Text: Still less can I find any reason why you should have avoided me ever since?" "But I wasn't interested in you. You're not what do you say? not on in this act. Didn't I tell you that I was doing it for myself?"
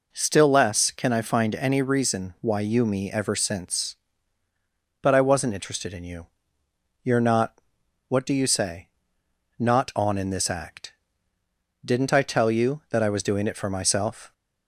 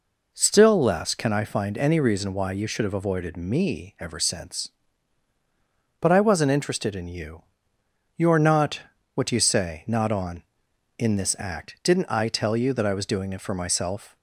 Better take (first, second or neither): second